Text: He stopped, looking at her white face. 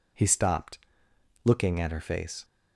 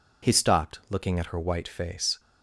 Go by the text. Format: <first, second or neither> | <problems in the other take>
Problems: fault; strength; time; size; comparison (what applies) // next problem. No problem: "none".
second | skips "white"; at 2.0 s